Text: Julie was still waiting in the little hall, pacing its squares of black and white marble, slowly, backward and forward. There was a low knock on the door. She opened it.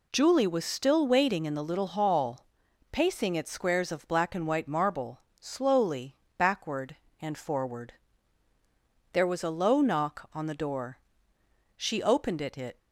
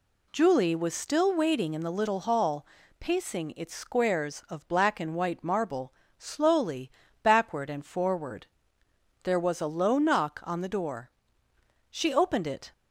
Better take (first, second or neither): second